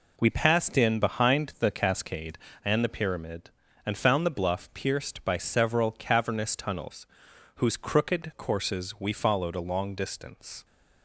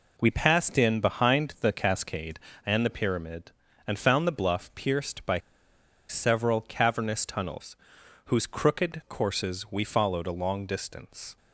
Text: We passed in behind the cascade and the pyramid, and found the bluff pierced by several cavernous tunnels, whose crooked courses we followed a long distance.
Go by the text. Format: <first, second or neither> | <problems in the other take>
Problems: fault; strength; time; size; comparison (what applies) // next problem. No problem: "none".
first | pauses between "by" and "several"; noticeable; at 5.3 s; 0.71 s long